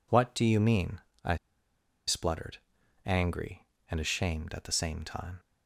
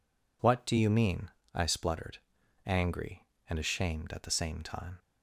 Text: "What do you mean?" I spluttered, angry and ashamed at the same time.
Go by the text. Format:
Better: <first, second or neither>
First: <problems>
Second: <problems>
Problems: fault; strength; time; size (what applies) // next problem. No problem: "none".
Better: second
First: pauses between "I" and "spluttered"; noticeable; at 1.3 s; 0.71 s long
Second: none